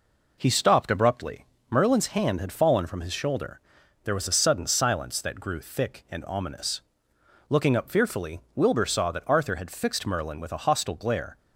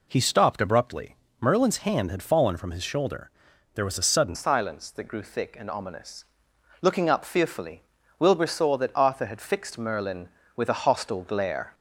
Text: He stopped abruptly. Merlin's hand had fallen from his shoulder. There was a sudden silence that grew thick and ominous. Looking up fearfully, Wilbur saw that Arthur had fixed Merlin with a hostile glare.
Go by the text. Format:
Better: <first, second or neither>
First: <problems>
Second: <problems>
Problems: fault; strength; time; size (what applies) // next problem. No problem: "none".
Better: first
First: none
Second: changes voice at "silence"; from 4.3 s on; 7.4 s long